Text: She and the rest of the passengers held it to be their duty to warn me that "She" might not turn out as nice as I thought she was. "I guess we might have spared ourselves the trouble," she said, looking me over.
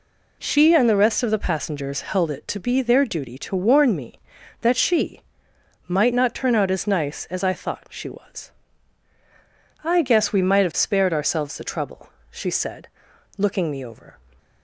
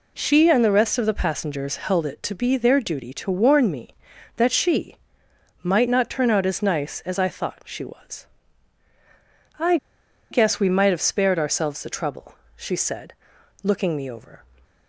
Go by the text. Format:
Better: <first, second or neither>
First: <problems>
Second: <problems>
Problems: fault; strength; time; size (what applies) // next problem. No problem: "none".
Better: first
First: pauses between "She" and "might"; noticeable; at 5.2 s; 0.68 s long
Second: pauses between "She" and "might"; noticeable; at 4.9 s; 0.68 s long // pauses between "I" and "guess"; noticeable; at 9.7 s; 0.55 s long